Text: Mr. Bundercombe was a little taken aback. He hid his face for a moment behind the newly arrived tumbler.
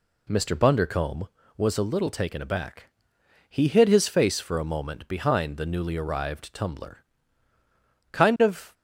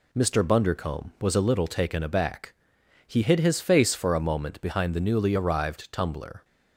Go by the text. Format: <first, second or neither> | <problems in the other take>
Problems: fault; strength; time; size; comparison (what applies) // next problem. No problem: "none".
second | goes on to say "Kind of"; noticeable; from 8.1 s on; 0.61 s long